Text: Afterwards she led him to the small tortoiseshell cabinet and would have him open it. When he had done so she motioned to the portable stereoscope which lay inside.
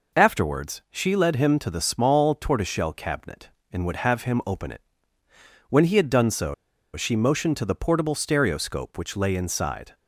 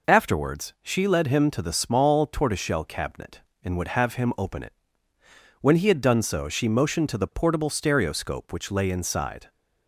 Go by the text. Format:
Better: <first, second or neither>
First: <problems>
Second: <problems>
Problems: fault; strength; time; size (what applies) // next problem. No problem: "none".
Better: second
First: pauses between "so" and "she"; at 6.5 s; 0.39 s long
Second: none